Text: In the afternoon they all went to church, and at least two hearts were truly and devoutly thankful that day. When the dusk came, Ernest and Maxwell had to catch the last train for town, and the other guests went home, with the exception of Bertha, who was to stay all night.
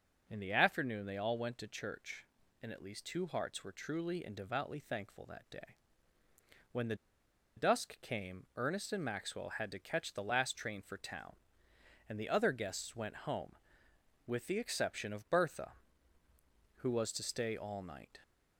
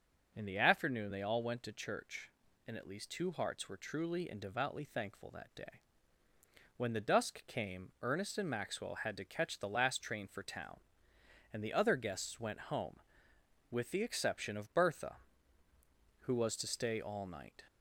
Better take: second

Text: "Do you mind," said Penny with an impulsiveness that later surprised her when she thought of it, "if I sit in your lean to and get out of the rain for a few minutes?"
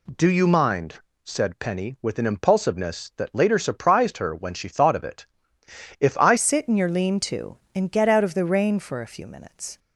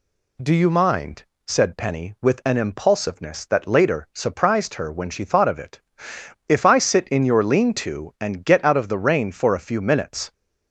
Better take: second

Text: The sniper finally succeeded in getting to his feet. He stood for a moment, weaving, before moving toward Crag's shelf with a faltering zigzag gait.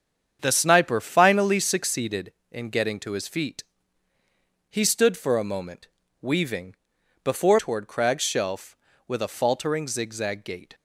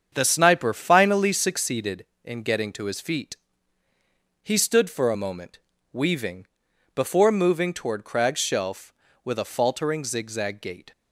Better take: second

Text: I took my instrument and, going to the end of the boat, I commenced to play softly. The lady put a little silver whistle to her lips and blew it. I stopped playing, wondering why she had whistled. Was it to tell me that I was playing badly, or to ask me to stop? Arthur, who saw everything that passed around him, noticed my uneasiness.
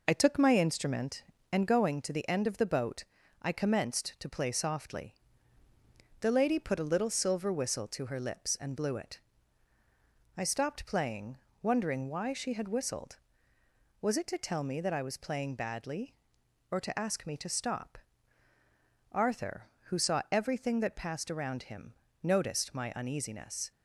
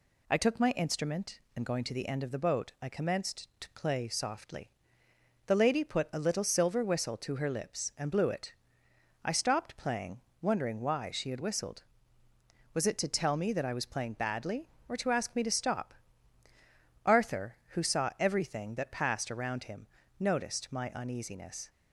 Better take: second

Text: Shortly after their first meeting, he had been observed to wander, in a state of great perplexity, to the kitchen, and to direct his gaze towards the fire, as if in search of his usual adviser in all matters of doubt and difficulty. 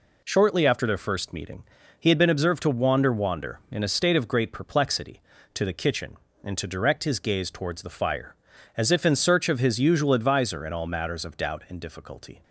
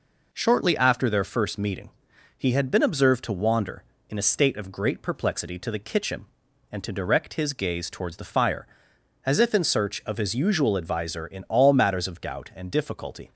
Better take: second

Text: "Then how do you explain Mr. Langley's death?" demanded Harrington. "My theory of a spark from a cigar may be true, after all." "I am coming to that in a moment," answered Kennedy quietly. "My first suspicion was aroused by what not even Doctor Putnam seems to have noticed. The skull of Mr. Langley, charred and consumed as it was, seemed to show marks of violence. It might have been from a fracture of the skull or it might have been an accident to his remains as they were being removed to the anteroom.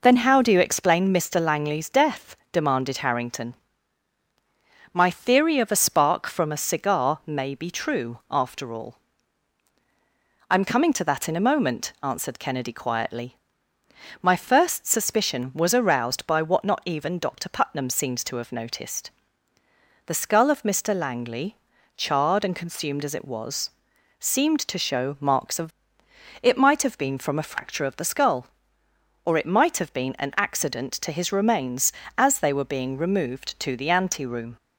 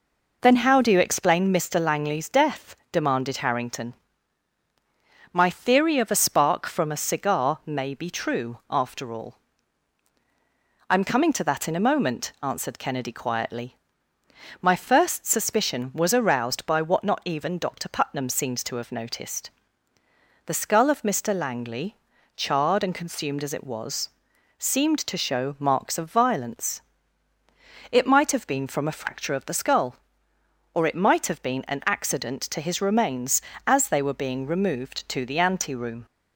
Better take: second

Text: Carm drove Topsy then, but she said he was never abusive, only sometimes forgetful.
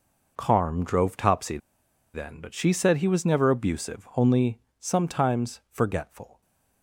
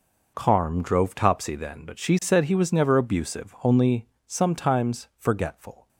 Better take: second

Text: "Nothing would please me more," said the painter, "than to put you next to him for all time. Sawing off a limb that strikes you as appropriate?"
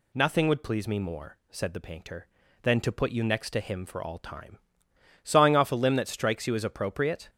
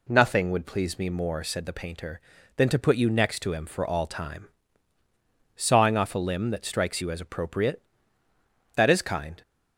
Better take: first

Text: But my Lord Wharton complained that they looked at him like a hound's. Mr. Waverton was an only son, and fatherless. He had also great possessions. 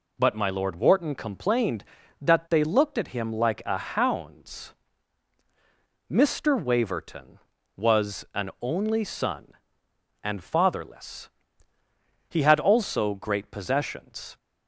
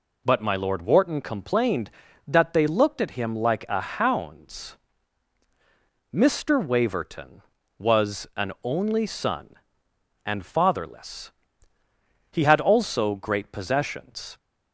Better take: neither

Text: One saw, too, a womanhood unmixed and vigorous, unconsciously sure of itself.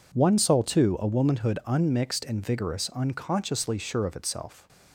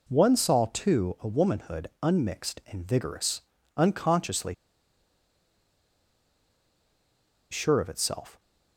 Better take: first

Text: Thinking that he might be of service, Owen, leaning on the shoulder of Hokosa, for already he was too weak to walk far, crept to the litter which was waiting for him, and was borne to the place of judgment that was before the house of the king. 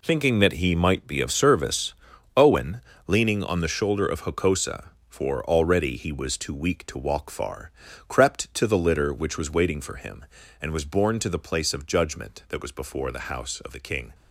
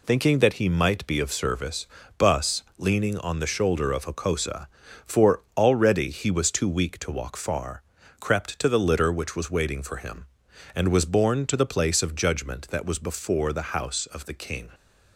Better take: first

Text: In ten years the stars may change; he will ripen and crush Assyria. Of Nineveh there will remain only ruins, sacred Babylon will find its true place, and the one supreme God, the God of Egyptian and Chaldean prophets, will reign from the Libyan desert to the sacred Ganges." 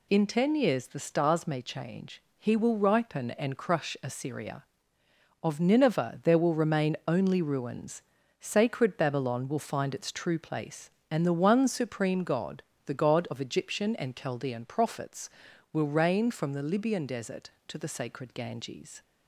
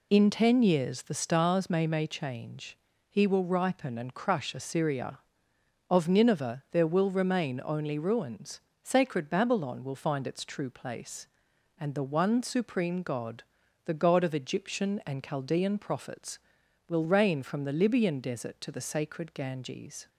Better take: first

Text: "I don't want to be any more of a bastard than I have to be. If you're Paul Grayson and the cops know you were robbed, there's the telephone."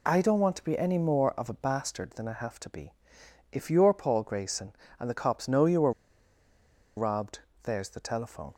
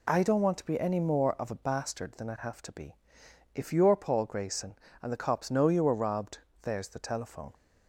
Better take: second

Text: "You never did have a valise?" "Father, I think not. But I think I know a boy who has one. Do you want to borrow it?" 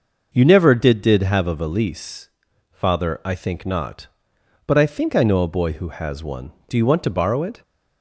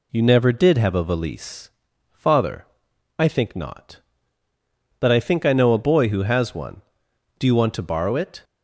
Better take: second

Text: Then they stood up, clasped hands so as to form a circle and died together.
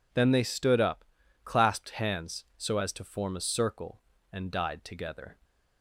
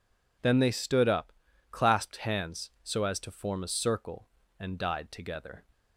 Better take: neither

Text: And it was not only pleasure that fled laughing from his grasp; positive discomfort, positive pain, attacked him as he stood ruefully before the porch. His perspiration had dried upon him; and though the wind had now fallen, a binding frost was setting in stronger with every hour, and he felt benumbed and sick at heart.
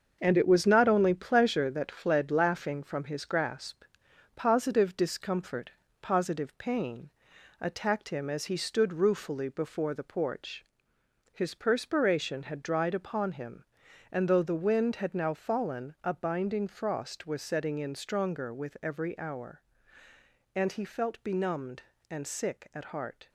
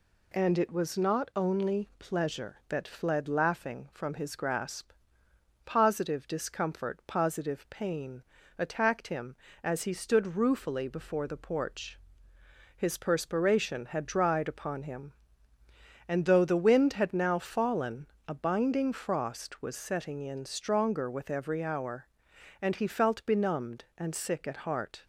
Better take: second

